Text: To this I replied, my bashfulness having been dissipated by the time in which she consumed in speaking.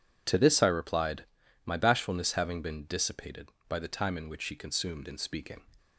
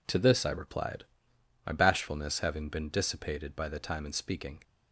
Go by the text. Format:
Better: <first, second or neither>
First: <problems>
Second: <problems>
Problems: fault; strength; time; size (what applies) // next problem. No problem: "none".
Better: first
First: none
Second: skips "in which she consumed"; at 4.0 s